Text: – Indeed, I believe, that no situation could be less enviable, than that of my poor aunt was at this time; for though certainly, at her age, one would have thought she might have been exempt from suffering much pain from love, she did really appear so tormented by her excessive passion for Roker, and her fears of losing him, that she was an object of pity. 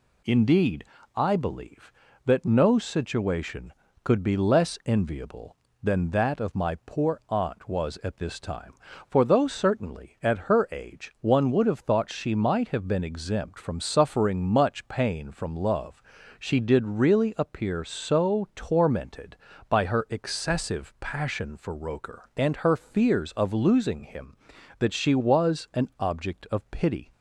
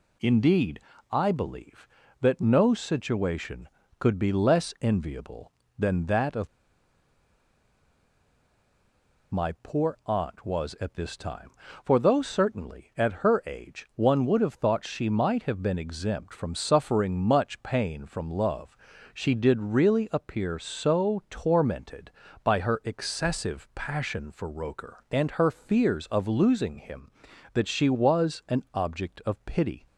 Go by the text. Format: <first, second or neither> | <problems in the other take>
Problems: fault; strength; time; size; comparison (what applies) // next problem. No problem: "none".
first | pauses between "of" and "my"; strong; at 6.4 s; 2.8 s long